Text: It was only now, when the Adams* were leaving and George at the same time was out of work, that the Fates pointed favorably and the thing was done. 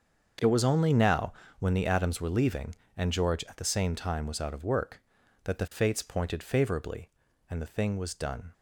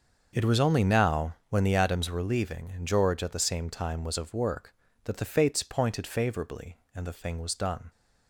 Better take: first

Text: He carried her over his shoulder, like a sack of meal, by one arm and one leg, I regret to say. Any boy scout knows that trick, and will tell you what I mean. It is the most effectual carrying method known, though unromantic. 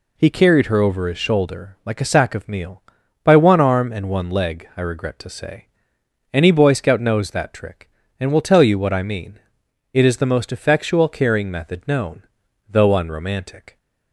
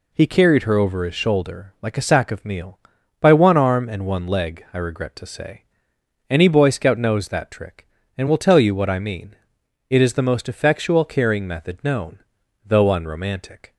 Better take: neither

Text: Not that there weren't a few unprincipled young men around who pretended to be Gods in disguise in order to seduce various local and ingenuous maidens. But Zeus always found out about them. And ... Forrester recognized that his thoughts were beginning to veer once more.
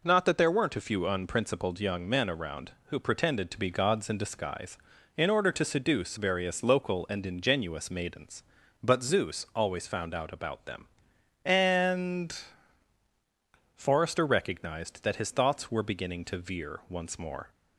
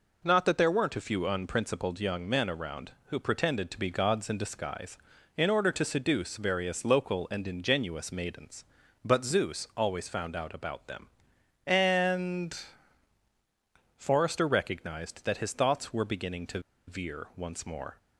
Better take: first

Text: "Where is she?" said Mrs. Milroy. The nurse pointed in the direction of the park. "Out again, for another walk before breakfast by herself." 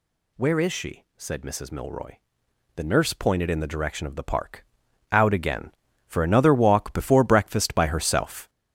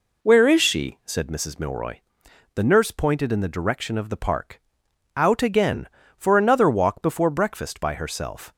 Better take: second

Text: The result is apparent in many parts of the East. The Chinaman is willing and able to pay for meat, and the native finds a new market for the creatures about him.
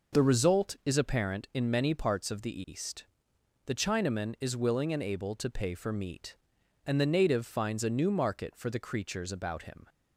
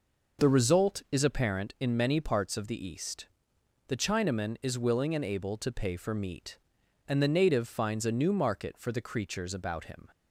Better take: neither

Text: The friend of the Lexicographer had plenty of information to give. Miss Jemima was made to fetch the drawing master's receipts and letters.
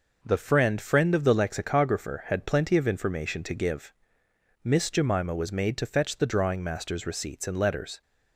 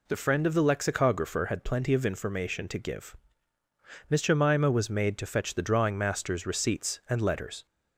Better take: second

